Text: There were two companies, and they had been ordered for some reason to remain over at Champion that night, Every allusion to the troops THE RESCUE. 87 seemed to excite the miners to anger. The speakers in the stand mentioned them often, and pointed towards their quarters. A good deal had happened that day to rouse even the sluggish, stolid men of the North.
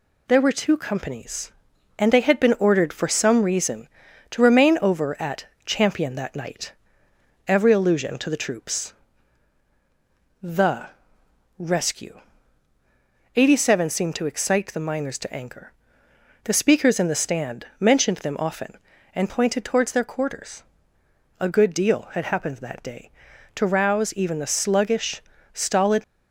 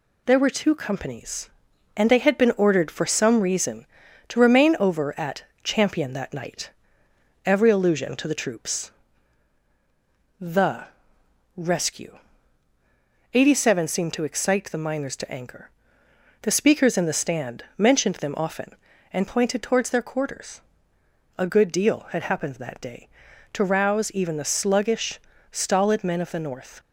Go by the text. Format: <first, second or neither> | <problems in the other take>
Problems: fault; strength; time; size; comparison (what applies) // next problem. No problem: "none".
second | pauses between "at" and "Champion"; slight; at 5.4 s; 0.20 s long; slight in the second // pauses between "troops" and "THE"; strong; at 8.9 s; 1.5 s long; strong in the second // pauses between "THE" and "RESCUE"; noticeable; at 10.8 s; 0.72 s long; noticeable in the second // stops before "men of the North"; at 26.0 s